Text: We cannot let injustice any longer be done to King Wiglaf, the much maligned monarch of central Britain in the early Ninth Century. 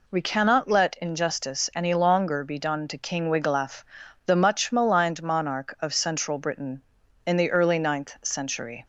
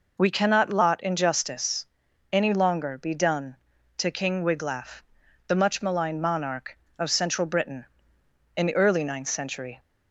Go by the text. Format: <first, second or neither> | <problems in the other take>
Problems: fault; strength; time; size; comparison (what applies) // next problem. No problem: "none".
first | says "lot" for "let"; at 0.7 s // pauses between "injustice" and "any"; noticeable; at 1.8 s; 0.46 s long